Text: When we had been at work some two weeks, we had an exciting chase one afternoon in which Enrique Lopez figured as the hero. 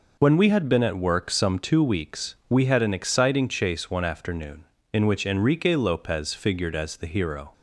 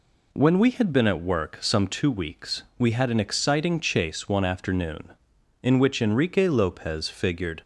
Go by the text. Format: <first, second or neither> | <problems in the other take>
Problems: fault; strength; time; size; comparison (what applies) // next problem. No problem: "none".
first | stops before "as the hero"; at 7.6 s